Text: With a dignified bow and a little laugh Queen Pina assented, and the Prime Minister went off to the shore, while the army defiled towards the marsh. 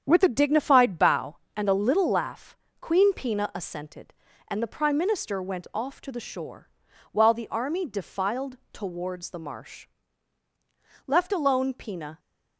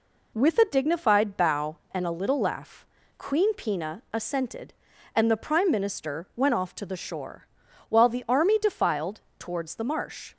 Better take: second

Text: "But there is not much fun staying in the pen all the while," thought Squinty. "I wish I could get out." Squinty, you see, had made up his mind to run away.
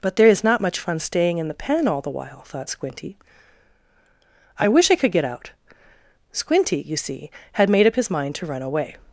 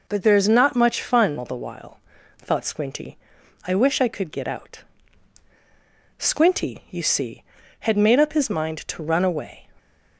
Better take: first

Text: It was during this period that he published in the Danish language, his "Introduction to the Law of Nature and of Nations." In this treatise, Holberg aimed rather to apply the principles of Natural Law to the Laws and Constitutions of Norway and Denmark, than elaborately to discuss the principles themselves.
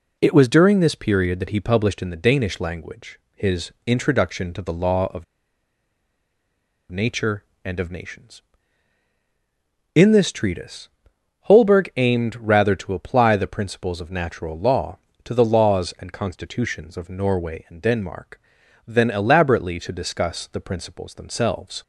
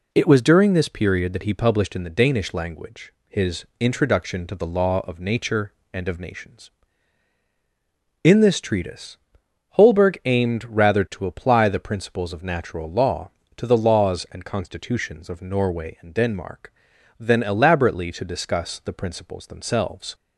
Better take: second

